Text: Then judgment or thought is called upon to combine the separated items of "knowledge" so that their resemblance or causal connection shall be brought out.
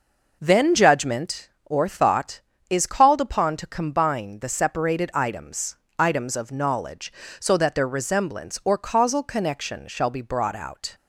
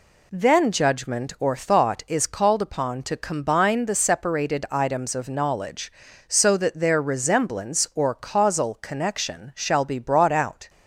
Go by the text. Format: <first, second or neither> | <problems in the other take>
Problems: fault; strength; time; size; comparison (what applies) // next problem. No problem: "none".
second | says "items" twice; at 5.9 s